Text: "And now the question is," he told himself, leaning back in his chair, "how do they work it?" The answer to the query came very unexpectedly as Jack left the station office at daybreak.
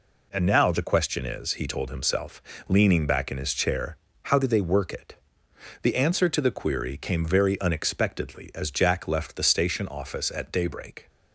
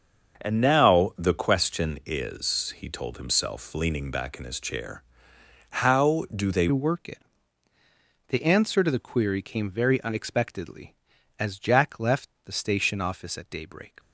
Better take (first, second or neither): first